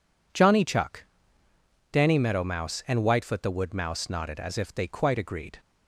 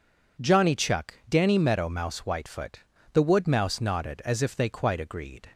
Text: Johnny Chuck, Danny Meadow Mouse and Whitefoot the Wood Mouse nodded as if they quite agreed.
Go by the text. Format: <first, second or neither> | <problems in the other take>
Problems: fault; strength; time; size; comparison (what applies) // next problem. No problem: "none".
first | skips "and"; at 2.2 s // pauses between "Whitefoot" and "the"; slight; at 2.7 s; 0.34 s long